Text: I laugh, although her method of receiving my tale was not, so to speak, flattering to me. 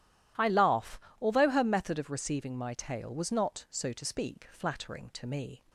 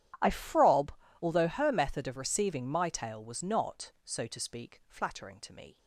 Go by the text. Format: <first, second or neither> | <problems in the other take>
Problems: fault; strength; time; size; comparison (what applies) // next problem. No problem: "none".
first | starts louder than the rest; strong; until 1.5 s; 11.5 dB // says "frob" for "laugh"; at 0.3 s